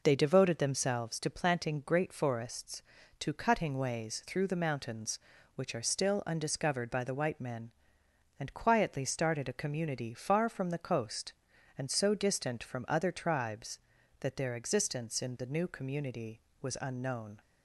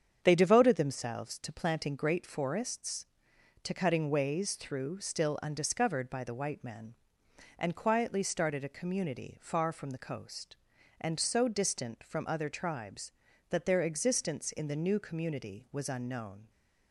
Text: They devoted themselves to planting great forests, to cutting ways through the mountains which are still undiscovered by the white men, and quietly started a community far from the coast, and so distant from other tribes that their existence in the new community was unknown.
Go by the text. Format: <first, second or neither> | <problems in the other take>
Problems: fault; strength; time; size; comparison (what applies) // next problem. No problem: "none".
first | starts louder than the rest; strong; until 1.2 s; 8 dB // skips "the mountains which are"; at 5.0 s